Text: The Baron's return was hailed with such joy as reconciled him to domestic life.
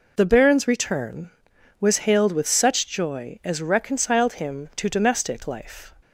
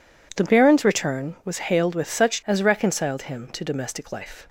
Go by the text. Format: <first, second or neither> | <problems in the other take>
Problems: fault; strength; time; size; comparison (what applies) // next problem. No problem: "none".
first | skips "joy"; at 2.4 s